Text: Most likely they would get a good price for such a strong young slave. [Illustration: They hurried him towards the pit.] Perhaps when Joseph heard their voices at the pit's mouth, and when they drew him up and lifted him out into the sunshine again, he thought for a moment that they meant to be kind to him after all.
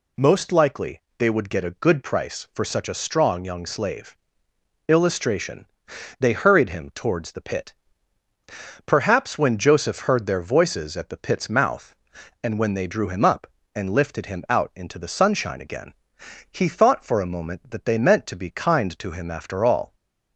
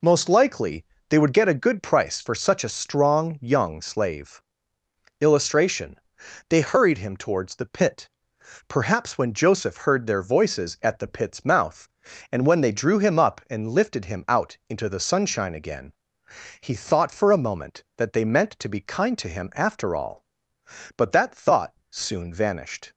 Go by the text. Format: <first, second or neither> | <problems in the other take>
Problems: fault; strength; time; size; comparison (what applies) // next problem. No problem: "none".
first | pauses between "likely" and "they"; slight; at 0.8 s; 0.24 s long; slight in the first // goes on to say "But that thought soon vanished"; strong; from 20.9 s on; 1.9 s long